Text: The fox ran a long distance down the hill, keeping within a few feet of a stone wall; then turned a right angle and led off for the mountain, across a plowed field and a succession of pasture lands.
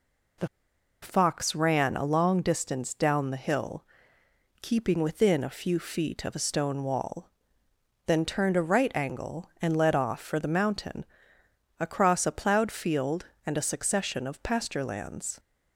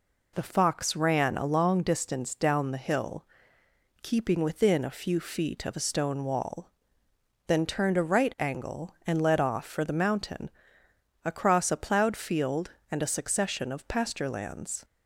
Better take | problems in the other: second | pauses between "The" and "fox"; noticeable; at 0.4 s; 0.55 s long

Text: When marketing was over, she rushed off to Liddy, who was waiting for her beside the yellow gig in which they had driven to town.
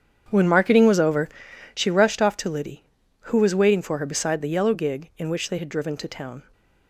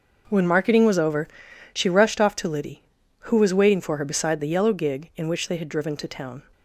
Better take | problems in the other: second | starts louder than the rest; strong; until 1.8 s; 8 dB

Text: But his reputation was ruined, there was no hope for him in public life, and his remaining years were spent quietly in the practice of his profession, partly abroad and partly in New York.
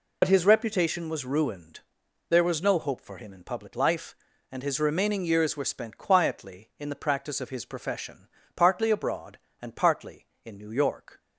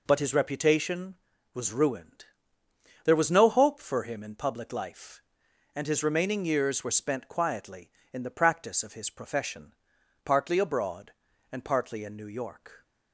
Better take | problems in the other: second | loses the start of "But"; at 0.2 s; 65 ms

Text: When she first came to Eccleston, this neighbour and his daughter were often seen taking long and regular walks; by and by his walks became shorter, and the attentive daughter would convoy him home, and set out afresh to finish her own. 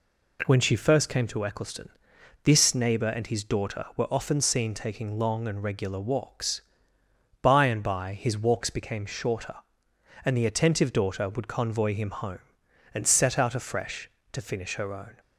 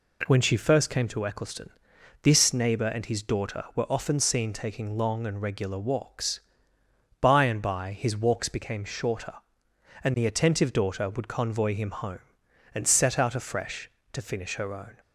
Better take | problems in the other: neither | none

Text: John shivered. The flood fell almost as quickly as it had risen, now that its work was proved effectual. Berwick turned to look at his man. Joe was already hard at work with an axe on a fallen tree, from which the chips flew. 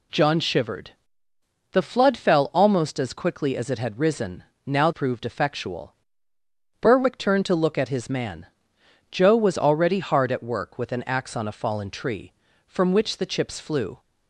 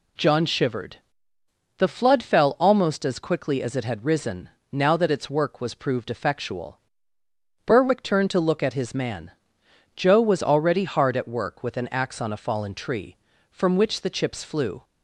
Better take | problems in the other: second | skips "that its work was"; at 4.9 s

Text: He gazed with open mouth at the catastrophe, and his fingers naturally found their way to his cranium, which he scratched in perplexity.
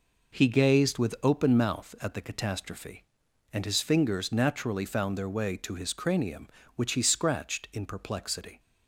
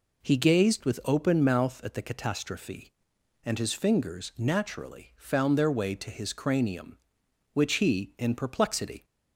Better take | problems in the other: first | skips "scratched"; at 8.1 s

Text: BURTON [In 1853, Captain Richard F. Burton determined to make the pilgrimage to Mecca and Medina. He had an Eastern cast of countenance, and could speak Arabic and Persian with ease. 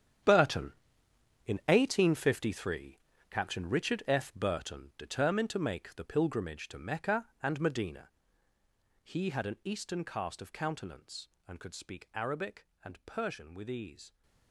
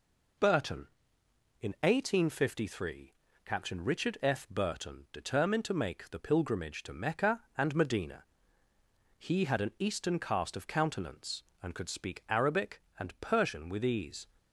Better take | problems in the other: second | gets quieter; strong; throughout; 14 dB

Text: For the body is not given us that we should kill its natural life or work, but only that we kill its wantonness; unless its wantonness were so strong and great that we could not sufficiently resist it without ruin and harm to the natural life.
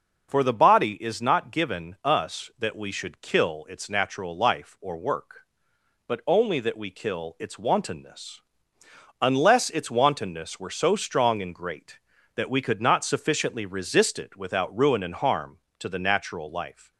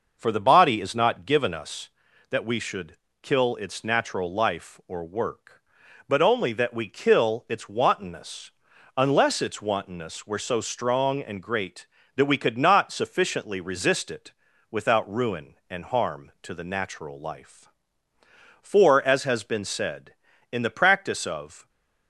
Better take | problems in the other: first | pauses between "should" and "kill"; slight; at 2.9 s; 0.26 s long // pauses between "it" and "without"; at 14.3 s; 0.40 s long // goes on to say "For as has been said in the practice of"; strong; from 18.6 s on; 3.0 s long

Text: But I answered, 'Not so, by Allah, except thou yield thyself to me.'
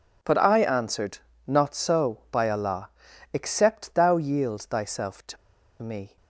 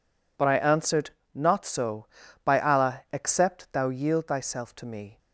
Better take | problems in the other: second | pauses between "to" and "me"; at 5.3 s; 0.45 s long

